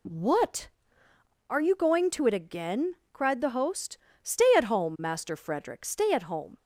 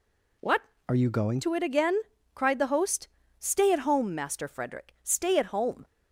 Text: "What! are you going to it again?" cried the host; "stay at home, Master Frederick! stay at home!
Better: first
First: none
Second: changes voice from "are" to "going"; from 0.8 to 1.4 s; 0.6 s long

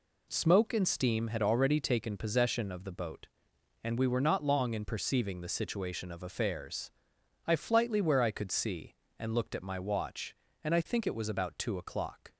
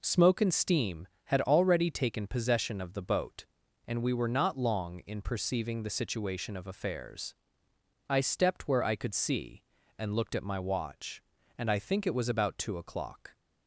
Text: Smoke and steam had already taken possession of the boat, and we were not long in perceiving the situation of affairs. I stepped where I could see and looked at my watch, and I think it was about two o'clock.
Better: second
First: says "flightly" for "stepped"; at 7.5 s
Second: none

